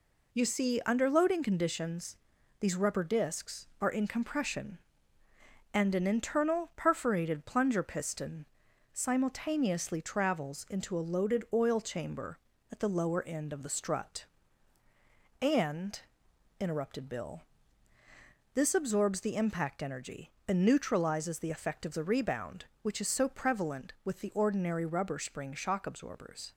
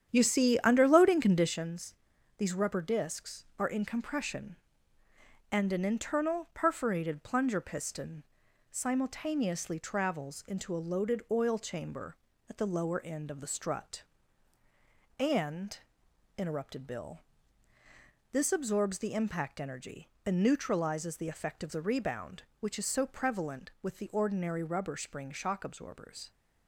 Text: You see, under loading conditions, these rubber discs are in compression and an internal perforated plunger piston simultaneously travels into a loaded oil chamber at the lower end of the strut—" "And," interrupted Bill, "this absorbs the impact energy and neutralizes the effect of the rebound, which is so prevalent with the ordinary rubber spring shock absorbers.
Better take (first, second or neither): first